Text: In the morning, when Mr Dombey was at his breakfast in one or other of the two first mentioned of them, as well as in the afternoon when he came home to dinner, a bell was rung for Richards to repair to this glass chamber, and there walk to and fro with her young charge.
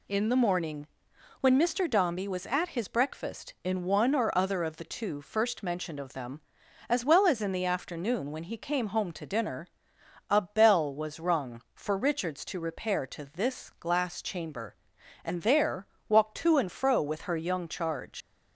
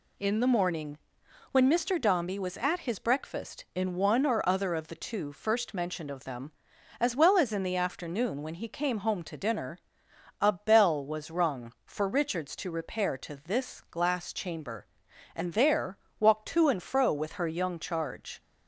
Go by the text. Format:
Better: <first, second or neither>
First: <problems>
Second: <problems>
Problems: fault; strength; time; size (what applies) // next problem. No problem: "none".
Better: second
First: pauses between "there" and "walk"; slight; at 15.8 s; 0.20 s long // leaves "charge" unfinished; at 18.2 s; 85 ms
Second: pauses between "there" and "walk"; slight; at 15.9 s; 0.20 s long